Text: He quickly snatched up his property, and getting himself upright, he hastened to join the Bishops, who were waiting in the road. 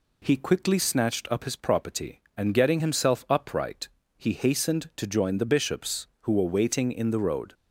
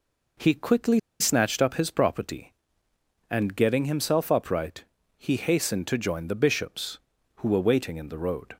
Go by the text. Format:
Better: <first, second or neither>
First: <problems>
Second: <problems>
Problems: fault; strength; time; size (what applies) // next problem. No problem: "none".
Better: first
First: none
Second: pauses between "quickly" and "snatched"; slight; at 0.9 s; 0.20 s long